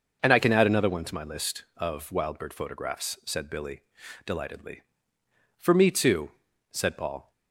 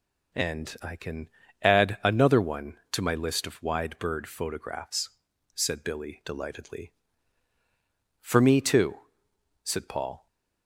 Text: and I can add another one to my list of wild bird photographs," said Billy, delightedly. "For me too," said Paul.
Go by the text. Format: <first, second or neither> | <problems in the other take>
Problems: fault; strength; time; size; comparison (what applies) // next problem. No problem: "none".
first | pauses between "can" and "add"; slight; at 1.2 s; 0.34 s long // says "wide" for "wild"; at 3.6 s